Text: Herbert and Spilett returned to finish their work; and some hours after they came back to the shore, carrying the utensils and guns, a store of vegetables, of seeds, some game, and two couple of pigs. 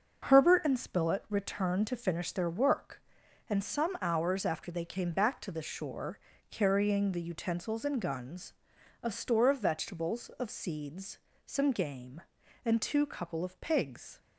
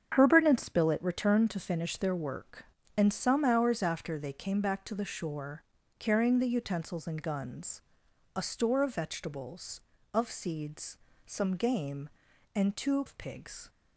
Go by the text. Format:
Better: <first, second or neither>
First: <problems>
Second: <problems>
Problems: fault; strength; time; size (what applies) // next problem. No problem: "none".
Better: first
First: starts louder than the rest; until 1.3 s; 6.5 dB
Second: starts louder than the rest; strong; until 1.1 s; 7.5 dB // skips "couple"; at 13.0 s